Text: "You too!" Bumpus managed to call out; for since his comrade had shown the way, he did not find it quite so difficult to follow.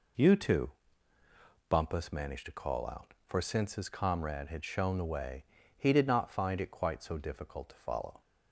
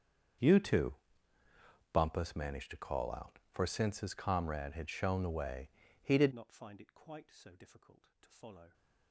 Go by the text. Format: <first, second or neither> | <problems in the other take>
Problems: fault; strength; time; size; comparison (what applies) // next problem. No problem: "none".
first | starts louder than the rest; strong; until 2.3 s; 7.5 dB // changes voice at "not"; from 6.3 s on; 2.4 s long